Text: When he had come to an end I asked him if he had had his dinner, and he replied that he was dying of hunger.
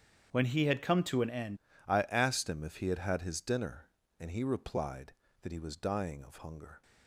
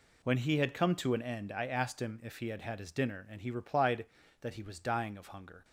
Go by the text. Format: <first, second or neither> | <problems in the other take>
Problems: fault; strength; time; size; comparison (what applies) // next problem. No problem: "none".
second | starts louder than the rest; strong; until 1.3 s; 8 dB // changes voice at "I"; from 1.8 s on; 5.0 s long